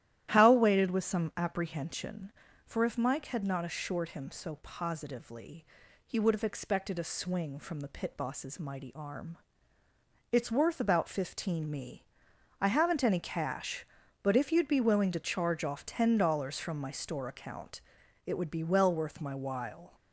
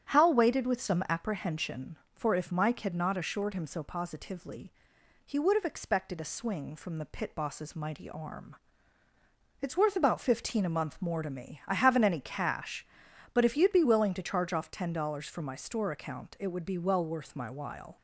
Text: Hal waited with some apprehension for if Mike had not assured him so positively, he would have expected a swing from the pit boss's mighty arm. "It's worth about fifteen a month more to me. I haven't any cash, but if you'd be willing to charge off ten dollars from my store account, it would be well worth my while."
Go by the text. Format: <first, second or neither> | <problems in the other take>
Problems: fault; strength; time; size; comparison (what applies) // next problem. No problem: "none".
second | starts louder than the rest; strong; until 1.3 s; 12.5 dB; strong in the second // skips "a month more to"; at 11.6 s